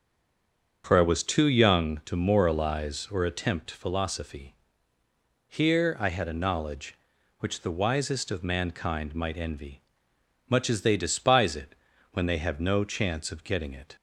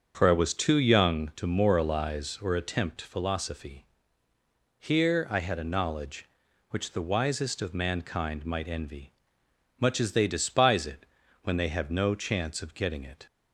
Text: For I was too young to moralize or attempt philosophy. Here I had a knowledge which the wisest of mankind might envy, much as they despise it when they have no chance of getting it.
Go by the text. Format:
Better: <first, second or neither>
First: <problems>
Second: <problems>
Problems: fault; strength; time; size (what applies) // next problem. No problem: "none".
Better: second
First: stays silent before the first word; slight; until 0.8 s; 0.8 s long // starts louder than the rest; until 1.8 s; 7 dB // pauses between "it" and "when"; at 11.7 s; 0.38 s long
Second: starts louder than the rest; until 1.1 s; 7 dB // pauses between "it" and "when"; at 11.0 s; 0.38 s long